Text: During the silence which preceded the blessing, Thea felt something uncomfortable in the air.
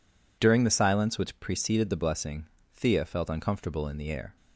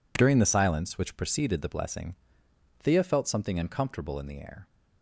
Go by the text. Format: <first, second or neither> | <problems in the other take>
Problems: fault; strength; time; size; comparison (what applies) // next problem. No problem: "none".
second | skips "something"; at 3.2 s